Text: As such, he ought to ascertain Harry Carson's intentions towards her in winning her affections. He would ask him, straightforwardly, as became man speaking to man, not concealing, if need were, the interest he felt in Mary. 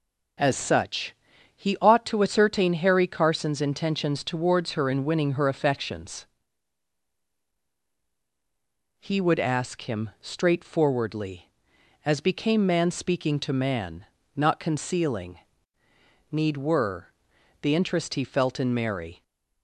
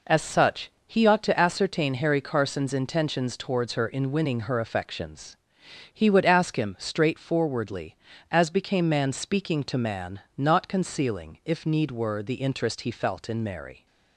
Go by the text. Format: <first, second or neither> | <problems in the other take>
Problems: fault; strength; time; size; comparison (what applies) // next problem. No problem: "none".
second | skips "if"; at 15.8 s